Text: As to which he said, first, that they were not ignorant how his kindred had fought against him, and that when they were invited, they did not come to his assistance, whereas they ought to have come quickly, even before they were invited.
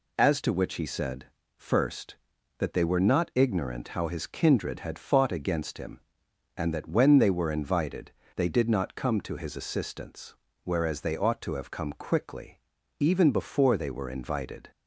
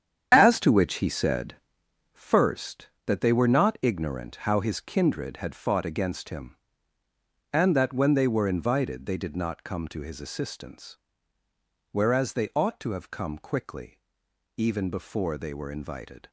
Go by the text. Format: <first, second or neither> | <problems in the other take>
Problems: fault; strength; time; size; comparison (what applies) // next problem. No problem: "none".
first | gets quieter; strong; throughout; 9.5 dB